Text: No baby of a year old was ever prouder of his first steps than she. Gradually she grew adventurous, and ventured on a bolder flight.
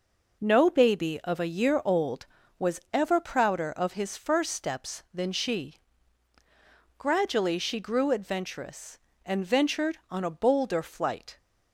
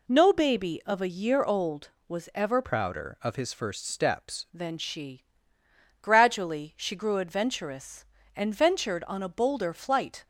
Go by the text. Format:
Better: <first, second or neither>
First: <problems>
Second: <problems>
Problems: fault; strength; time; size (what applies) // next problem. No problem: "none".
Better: first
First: none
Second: changes voice from "prouder" to "steps"; from 2.6 to 4.4 s; 1.8 s long